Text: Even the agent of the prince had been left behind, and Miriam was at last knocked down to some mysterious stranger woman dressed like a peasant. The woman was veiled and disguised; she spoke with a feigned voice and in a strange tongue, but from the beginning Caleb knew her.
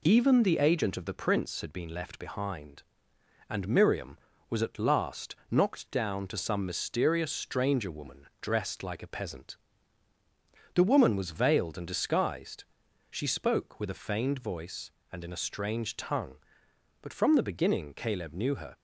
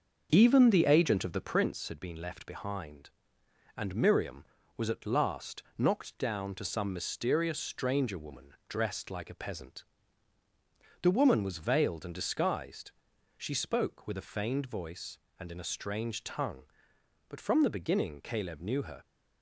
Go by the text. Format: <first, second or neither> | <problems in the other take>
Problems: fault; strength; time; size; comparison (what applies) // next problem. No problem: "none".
first | starts louder than the rest; until 1.7 s; 6.5 dB // pauses between "last" and "knocked"; slight; at 5.6 s; 0.16 s long; slight in the first